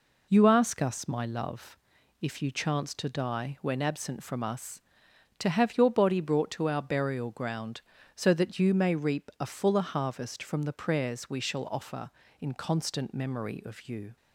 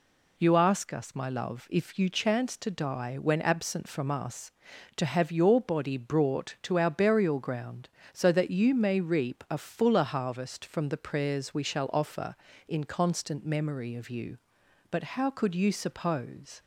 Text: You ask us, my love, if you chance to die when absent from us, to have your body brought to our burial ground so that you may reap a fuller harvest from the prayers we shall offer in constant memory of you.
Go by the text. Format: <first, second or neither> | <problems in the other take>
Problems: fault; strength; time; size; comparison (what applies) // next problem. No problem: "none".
first | goes on to say "But how could you suppose"; strong; from 14.9 s on; 1.7 s long